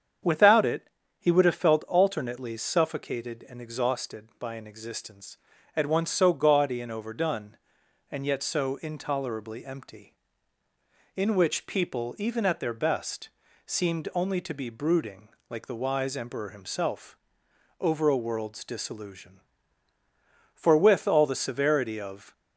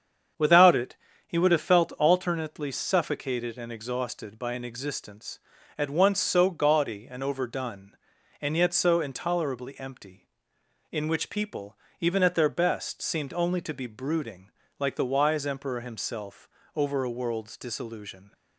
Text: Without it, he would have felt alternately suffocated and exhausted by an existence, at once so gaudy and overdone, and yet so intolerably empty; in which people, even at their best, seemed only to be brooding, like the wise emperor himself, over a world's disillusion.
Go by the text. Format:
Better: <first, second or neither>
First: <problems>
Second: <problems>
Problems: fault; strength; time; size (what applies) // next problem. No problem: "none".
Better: second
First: starts louder than the rest; strong; until 1.5 s; 7.5 dB // goes on to say "For with all the severity of"; strong; from 20.5 s on; 1.7 s long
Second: starts louder than the rest; strong; until 1.6 s; 7.5 dB